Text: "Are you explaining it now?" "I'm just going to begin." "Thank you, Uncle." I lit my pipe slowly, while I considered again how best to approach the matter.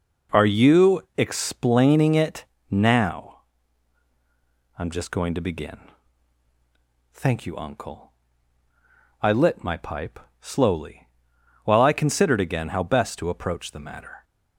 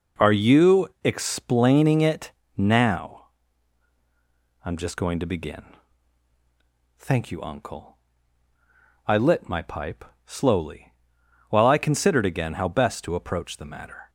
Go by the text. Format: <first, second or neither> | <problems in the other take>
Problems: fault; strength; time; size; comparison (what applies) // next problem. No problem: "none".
neither | pauses between "you" and "explaining"; slight; the same in both // pauses between "it" and "now"; slight; the same in both // pauses between "pipe" and "slowly"; slight; the same in both